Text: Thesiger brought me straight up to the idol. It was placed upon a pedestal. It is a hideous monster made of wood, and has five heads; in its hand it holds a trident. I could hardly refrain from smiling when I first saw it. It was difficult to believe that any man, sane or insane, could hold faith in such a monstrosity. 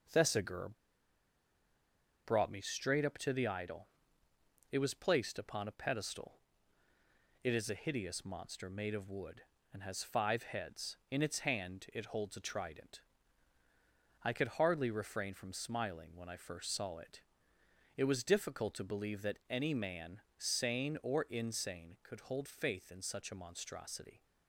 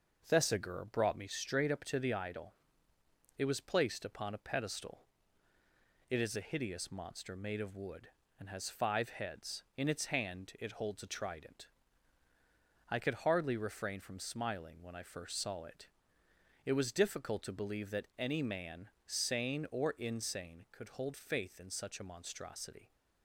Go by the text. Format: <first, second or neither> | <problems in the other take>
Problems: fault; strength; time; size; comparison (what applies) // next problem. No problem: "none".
second | pauses between "Thesiger" and "brought"; strong; at 0.6 s; 1.5 s long